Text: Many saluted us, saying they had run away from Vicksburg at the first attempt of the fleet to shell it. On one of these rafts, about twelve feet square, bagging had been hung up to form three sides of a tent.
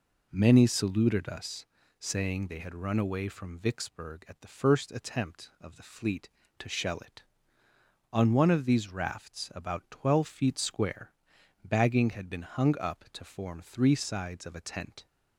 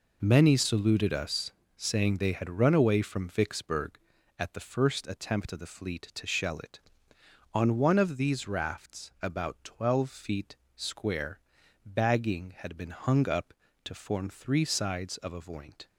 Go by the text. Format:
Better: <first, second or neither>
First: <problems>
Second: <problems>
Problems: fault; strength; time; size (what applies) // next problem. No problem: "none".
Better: first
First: none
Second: pauses between "feet" and "square"; slight; at 10.5 s; 0.20 s long // says "voint" for "tent"; at 15.4 s